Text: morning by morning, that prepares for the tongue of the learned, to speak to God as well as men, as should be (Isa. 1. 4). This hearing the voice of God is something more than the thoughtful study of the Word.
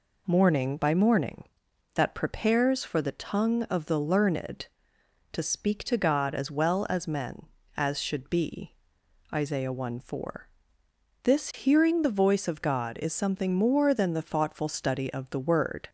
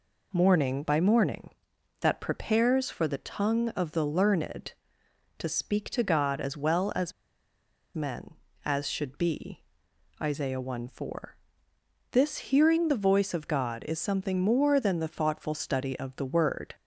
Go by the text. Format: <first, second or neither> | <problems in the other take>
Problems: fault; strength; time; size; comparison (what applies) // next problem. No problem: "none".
first | pauses between "as" and "men"; noticeable; at 7.1 s; 0.84 s long